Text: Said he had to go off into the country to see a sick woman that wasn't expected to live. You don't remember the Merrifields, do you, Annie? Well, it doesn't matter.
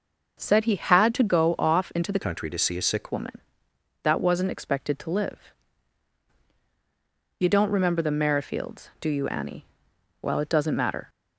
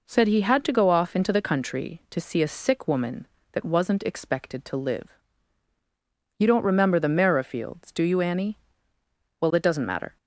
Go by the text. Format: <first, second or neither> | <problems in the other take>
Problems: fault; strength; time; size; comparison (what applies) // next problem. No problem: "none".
second | starts louder than the rest; until 1.4 s; 6.5 dB // changes voice from "country" to "sick"; from 2.2 to 3.0 s; 0.8 s long